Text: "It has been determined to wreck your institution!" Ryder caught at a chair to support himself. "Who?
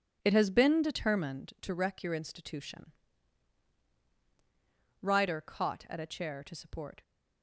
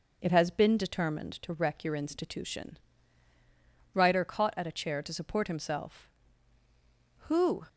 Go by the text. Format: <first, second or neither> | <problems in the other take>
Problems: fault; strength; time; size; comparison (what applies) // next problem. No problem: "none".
second | stops before "himself Who"; at 7.0 s